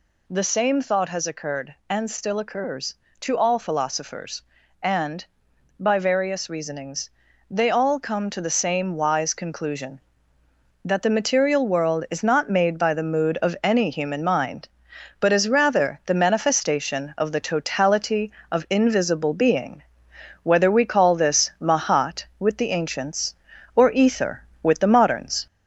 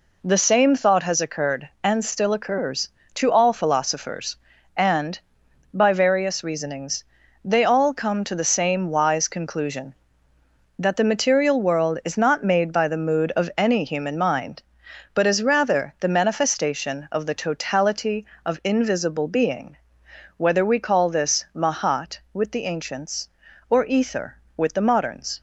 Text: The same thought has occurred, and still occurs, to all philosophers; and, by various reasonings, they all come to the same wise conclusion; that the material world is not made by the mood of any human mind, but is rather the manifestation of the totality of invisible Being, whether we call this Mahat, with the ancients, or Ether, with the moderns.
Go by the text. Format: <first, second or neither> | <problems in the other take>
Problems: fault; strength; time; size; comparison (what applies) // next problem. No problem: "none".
second | gets louder; slight; throughout; 2.5 dB